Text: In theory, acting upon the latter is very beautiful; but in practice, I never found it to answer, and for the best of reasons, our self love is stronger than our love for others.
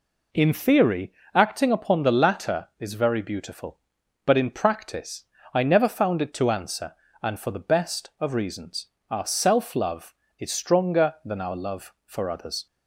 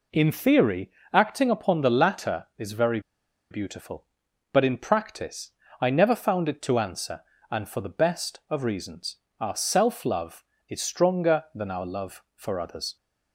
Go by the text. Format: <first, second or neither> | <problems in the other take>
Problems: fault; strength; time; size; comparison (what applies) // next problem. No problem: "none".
first | pauses between "very" and "beautiful"; noticeable; at 2.9 s; 0.51 s long